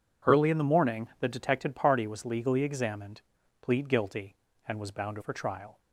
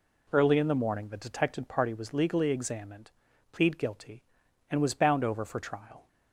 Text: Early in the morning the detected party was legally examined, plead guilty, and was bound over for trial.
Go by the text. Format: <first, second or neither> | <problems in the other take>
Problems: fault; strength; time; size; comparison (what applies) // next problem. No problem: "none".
second | skips "over"; at 5.1 s